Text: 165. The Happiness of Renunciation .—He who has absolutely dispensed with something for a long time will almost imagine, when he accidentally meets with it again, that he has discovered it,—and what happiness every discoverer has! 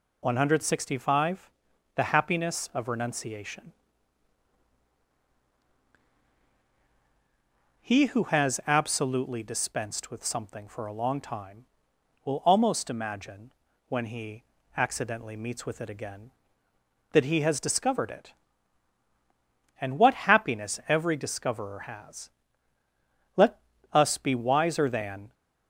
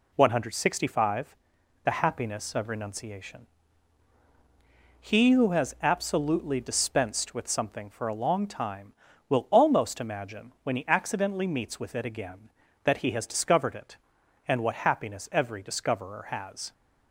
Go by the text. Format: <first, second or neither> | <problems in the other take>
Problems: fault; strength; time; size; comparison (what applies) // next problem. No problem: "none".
second | pauses between "he" and "accidentally"; slight; at 14.4 s; 0.34 s long // goes on to say "Let us be wiser than"; strong; from 23.3 s on; 1.9 s long